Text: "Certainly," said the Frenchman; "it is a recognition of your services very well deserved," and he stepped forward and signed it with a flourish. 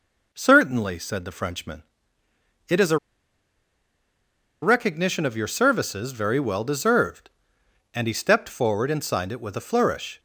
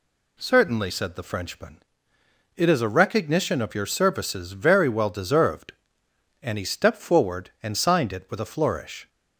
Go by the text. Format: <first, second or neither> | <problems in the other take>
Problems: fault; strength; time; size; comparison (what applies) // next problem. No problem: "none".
second | pauses between "a" and "recognition"; strong; at 2.9 s; 1.6 s long